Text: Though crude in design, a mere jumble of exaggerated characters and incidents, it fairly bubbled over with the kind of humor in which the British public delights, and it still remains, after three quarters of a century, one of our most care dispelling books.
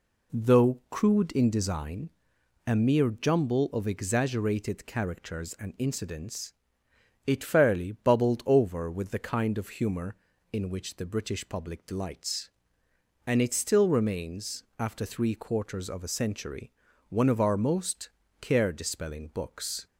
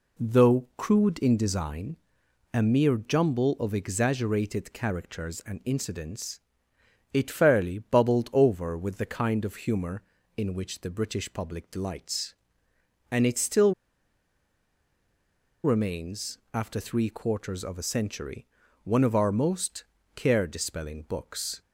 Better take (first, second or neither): first